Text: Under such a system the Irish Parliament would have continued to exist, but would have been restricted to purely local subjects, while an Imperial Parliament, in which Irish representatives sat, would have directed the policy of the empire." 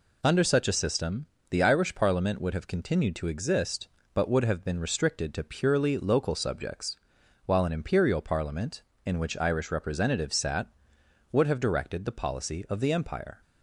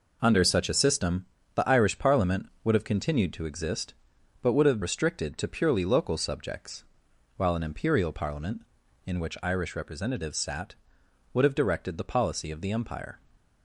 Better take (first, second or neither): first